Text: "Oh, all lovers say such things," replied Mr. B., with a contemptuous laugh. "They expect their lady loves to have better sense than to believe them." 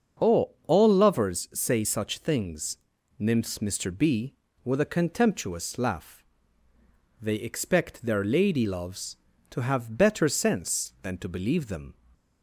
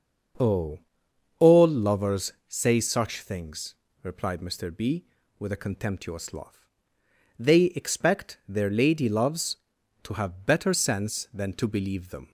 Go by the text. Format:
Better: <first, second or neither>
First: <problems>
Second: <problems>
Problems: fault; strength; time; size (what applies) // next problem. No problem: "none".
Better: second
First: starts louder than the rest; until 1.3 s; 6.5 dB // says "nymphs" for "replied"; at 3.1 s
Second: starts louder than the rest; until 1.9 s; 7 dB